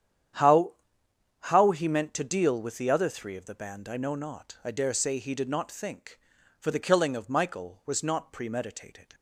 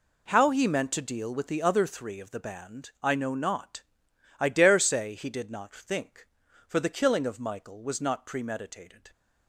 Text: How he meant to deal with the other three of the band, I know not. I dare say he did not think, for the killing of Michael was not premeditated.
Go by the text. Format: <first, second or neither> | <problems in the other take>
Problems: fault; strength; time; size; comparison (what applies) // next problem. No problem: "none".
second | starts louder than the rest; strong; until 2.0 s; 9.5 dB // says "How" twice; at 1.4 s